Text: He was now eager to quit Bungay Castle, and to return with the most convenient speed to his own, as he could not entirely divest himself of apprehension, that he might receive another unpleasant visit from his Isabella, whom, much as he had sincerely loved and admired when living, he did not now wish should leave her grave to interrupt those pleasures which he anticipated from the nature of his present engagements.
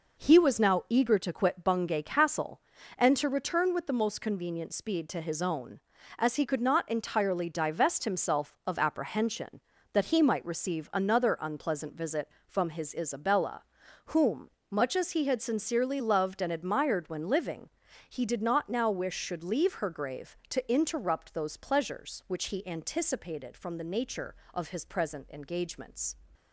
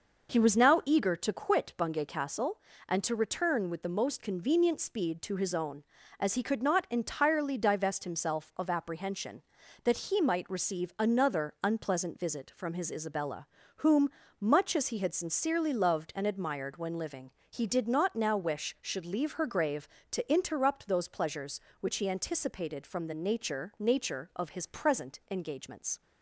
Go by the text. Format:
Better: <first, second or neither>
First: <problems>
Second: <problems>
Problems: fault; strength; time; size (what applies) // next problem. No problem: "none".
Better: first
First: none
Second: says "nature" twice; at 23.7 s